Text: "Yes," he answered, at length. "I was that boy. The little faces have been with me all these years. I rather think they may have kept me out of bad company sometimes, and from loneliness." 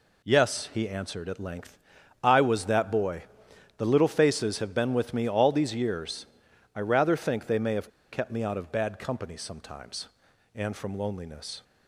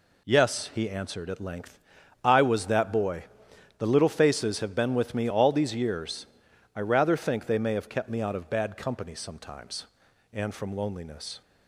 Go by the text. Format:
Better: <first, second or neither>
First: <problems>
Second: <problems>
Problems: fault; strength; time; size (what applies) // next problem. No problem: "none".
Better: second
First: pauses between "have" and "kept"; slight; at 7.8 s; 0.22 s long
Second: none